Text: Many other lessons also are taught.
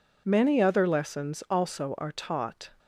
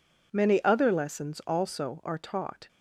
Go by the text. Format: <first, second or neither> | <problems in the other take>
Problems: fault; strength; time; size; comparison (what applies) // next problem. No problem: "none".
neither | none